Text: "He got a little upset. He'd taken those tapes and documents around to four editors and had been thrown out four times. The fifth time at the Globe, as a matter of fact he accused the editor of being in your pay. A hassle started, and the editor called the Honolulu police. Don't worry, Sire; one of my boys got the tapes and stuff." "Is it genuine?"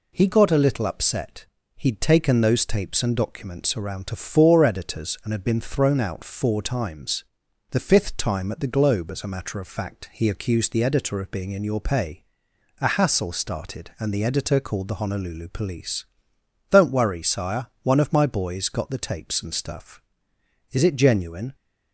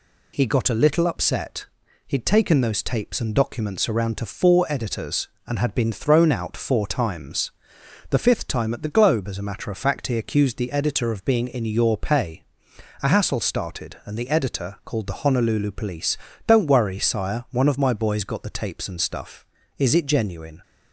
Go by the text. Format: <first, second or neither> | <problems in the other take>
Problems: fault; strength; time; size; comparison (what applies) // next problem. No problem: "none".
neither | none